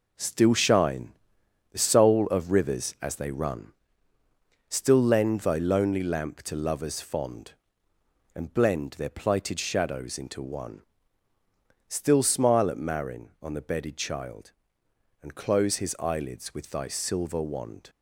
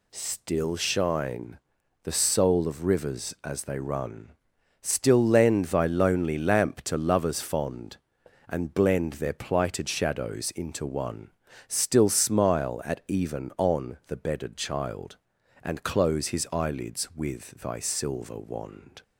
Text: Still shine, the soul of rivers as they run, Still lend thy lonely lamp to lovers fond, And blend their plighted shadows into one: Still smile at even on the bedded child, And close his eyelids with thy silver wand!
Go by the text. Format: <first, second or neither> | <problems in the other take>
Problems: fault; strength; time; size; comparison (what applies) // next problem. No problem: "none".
second | says "marin" for "even"; at 12.7 s